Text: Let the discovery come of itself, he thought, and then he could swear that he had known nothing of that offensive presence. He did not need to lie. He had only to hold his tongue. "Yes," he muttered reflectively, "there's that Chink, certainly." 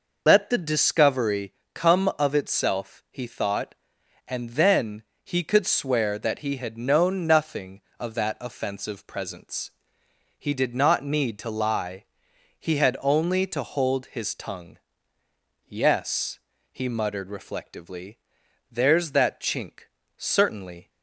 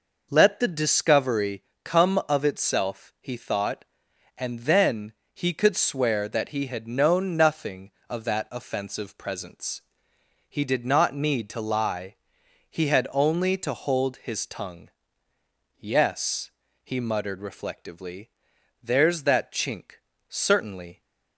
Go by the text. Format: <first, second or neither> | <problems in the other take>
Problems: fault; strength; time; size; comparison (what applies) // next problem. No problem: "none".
second | loses the start of "Let"; at 0.2 s; 60 ms // pauses between "discovery" and "come"; slight; at 1.5 s; 0.22 s long; slight in the second // pauses between "then" and "he"; slight; at 5.0 s; 0.22 s long; slight in the second